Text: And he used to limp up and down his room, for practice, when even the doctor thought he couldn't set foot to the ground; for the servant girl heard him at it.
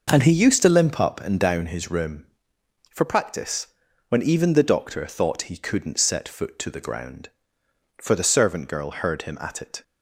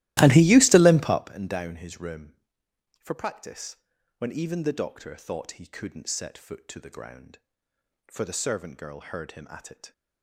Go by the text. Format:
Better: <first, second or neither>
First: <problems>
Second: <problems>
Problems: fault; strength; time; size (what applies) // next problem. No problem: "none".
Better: first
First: none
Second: starts louder than the rest; strong; until 1.4 s; 16.5 dB